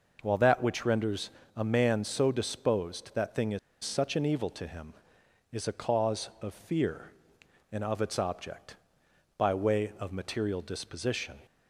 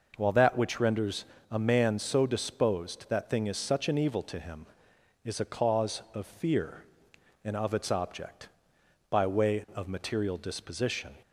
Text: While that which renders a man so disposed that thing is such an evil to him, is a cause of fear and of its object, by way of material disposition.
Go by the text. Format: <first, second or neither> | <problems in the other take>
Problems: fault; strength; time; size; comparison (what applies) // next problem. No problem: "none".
second | pauses between "renders" and "a"; slight; at 1.3 s; 0.26 s long; slight in the second // pauses between "is" and "such"; slight; at 3.5 s; 0.25 s long